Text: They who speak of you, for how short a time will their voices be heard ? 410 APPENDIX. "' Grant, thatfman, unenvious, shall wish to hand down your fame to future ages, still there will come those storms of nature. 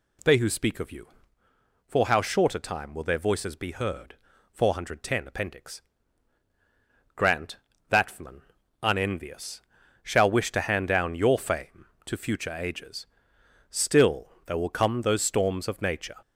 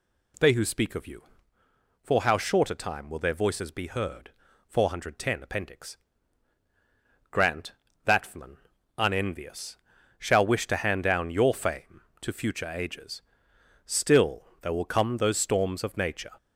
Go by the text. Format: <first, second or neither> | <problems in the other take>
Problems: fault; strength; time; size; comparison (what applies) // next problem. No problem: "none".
neither | none